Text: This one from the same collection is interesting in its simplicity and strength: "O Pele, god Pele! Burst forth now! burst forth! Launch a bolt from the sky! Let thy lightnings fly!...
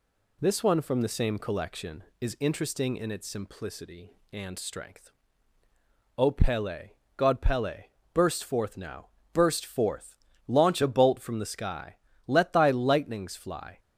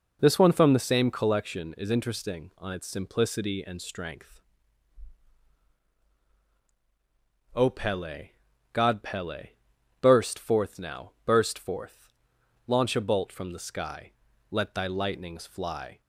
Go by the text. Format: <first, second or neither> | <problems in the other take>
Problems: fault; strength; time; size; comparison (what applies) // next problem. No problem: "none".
first | says "on" for "in"; at 2.5 s